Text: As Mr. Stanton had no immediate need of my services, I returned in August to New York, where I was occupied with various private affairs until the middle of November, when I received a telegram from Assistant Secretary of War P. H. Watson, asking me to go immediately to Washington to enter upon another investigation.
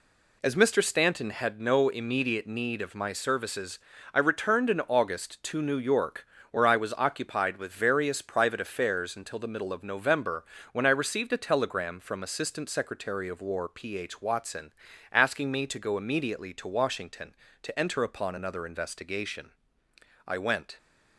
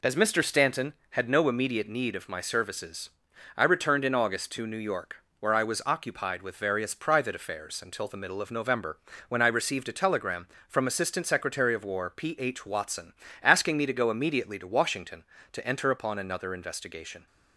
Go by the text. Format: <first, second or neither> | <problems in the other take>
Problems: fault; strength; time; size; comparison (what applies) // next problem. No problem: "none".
second | goes on to say "I went"; from 20.2 s on; 0.50 s long